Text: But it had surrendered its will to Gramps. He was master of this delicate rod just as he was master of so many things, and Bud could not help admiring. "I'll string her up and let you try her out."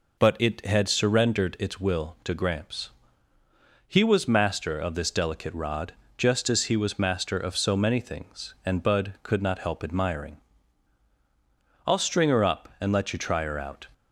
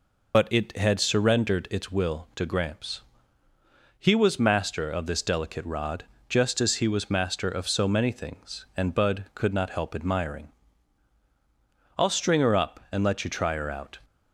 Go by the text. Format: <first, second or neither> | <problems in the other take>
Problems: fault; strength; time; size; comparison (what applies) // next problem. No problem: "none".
first | loses the start of "But"; at 0.3 s; 35 ms // pauses between "rod" and "just"; slight; at 6.0 s; 0.24 s long; slight in the first